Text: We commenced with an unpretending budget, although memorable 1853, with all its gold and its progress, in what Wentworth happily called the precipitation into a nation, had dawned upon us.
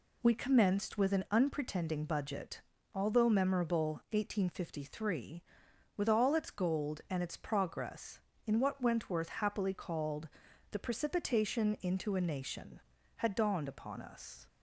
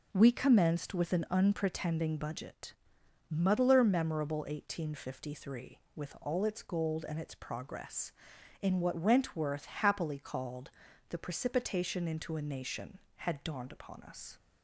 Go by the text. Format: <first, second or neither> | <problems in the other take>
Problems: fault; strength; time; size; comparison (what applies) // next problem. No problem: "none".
first | says "muddler" for "although"; at 3.3 s // pauses between "called" and "the"; at 10.7 s; 0.38 s long; also in the first